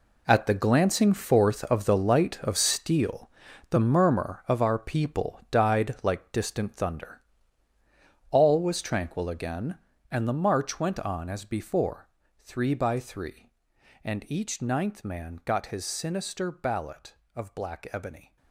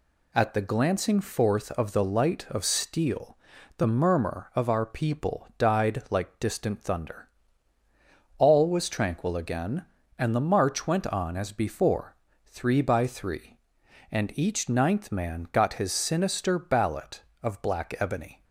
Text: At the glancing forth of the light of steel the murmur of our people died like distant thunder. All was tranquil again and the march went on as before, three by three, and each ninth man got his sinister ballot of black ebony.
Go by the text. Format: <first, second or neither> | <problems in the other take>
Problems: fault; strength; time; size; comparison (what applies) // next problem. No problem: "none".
second | gets quieter; strong; throughout; 13 dB // pauses between "steel" and "the"; at 3.2 s; 0.42 s long; also in the second